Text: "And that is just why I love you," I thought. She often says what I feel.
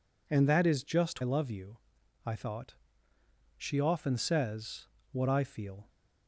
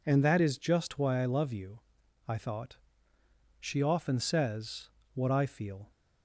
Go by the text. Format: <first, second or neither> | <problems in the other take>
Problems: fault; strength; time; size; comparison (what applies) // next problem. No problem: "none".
second | skips "why"; at 1.2 s // pauses between "says" and "what"; slight; at 4.8 s; 0.24 s long; slight in the second